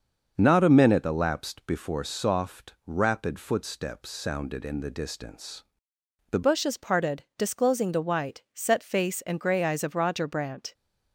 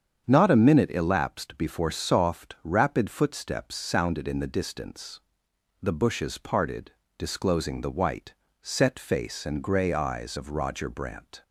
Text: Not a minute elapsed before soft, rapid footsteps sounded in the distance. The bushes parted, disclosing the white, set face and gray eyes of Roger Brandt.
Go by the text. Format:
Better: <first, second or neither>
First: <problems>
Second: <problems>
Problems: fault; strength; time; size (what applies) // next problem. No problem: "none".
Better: second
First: starts louder than the rest; until 1.3 s; 6.5 dB // changes voice at "bushes"; from 6.4 s on; 4.3 s long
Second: starts louder than the rest; strong; until 1.2 s; 7.5 dB